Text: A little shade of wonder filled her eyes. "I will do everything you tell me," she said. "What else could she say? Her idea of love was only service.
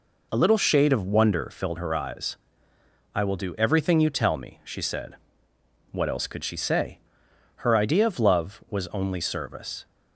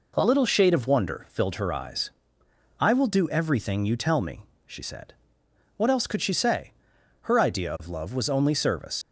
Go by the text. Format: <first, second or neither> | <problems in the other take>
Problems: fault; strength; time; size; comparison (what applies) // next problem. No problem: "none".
first | leaves "service" unfinished; at 9.0 s; 55 ms